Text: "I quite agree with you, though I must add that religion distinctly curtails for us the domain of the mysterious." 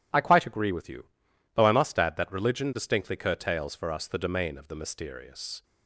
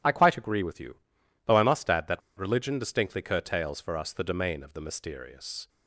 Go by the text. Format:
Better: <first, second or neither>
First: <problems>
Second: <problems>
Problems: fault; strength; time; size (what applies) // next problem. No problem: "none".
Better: first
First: none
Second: pauses between "that" and "religion"; slight; at 2.2 s; 0.18 s long